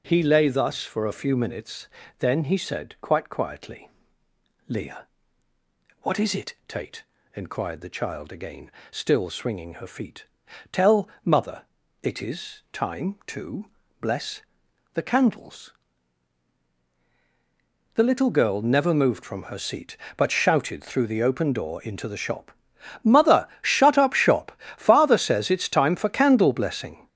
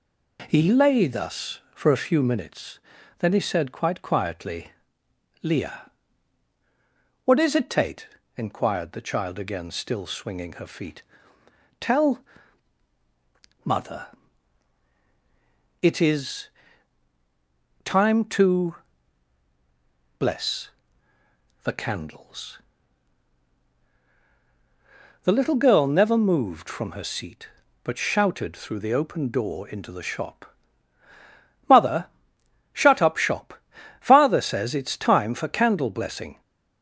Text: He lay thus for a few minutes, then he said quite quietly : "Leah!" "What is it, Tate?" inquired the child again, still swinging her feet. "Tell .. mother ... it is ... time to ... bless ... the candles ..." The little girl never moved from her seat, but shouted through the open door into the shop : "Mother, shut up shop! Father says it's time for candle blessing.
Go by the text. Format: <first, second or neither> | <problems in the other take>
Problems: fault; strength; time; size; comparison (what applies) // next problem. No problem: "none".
second | gets louder; throughout; 3.5 dB